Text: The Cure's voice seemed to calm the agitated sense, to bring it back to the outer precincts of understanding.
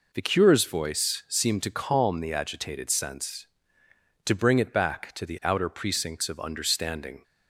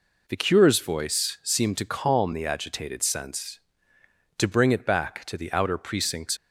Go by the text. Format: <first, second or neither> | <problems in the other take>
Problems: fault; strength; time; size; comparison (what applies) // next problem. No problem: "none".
first | stops before "of understanding"; at 6.3 s